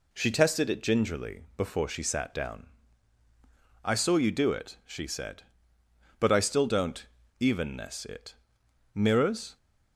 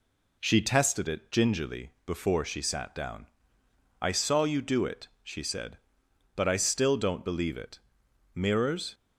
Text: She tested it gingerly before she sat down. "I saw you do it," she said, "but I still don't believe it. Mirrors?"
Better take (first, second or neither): second